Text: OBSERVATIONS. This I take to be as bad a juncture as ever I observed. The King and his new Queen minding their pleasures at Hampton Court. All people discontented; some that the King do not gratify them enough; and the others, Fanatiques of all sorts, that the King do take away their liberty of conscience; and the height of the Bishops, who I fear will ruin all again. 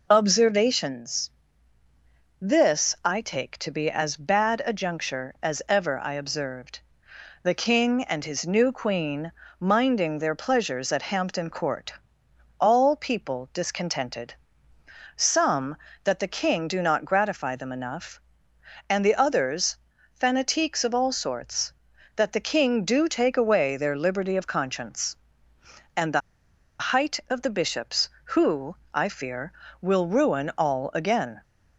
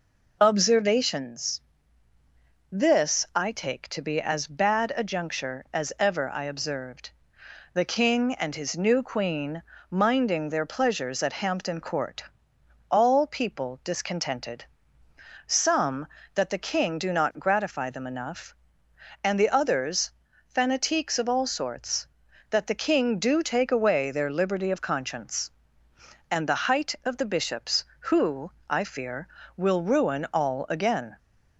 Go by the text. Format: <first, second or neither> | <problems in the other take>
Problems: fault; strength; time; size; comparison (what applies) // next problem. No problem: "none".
second | pauses between "Queen" and "minding"; slight; at 9.3 s; 0.26 s long; slight in the second // pauses between "the" and "height"; noticeable; at 26.2 s; 0.59 s long // pauses between "who" and "I"; slight; at 28.7 s; 0.20 s long; slight in the second